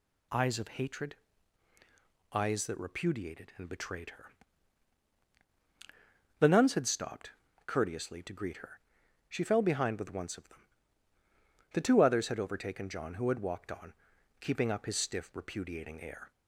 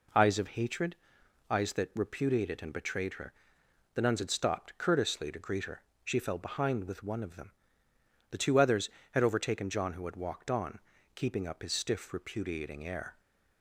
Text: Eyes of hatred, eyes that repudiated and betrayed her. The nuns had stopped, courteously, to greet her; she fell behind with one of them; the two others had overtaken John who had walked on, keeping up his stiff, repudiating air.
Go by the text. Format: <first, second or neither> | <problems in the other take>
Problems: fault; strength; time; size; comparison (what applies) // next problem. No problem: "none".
second | says "once" for "one"; at 10.1 s